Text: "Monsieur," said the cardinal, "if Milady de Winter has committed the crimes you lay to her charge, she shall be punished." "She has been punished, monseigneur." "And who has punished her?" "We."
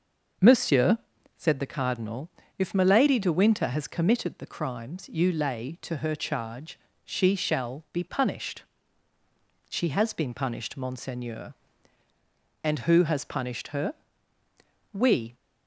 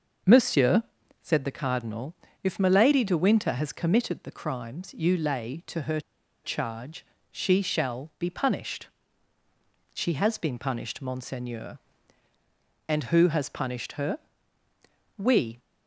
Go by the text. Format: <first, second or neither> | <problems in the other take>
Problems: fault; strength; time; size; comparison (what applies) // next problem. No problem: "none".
first | pauses between "her" and "charge"; at 5.9 s; 0.44 s long